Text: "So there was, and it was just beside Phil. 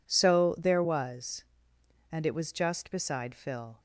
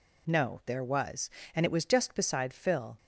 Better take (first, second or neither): first